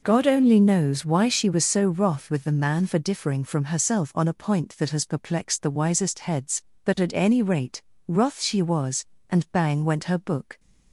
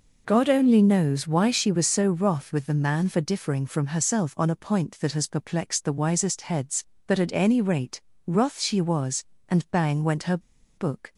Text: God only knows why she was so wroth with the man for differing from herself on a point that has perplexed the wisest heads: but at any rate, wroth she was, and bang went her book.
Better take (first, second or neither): first